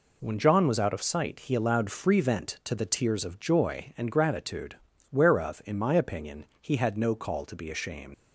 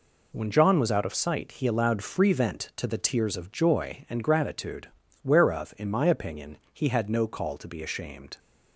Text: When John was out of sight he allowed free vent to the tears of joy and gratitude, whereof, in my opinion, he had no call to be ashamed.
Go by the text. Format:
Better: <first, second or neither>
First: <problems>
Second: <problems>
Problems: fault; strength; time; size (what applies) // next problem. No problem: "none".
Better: second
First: leaves "ashamed" unfinished; at 8.1 s; 115 ms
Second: none